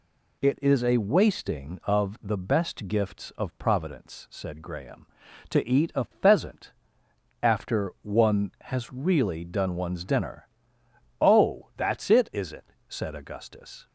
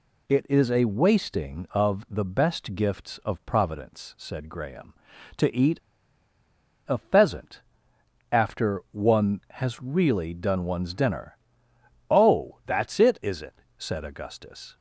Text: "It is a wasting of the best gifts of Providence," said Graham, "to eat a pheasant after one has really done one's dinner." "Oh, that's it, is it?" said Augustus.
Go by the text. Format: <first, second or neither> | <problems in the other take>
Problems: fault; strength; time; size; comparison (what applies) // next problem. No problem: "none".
first | pauses between "eat" and "a"; at 5.7 s; 1.1 s long // pauses between "pheasant" and "after"; noticeable; at 7.6 s; 0.68 s long; noticeable in the first